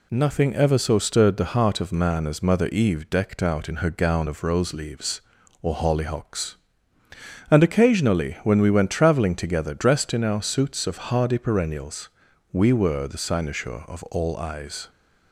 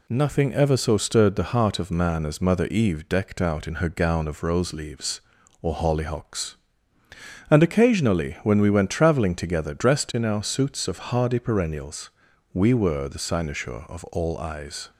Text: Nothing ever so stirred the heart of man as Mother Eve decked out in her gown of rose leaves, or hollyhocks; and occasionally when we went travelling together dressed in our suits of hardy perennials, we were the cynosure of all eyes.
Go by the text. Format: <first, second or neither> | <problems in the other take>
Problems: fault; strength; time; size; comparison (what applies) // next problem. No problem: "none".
neither | none